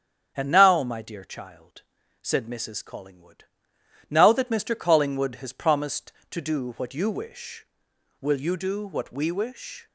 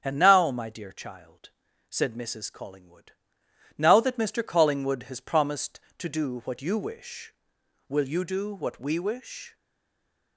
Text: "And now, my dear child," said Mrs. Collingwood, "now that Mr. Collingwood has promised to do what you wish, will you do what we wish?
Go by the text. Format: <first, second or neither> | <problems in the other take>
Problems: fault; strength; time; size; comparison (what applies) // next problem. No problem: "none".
first | starts louder than the rest; strong; until 1.0 s; 8.5 dB; strong in the first // stays silent after the last word; slight; from 9.5 s on; 0.8 s long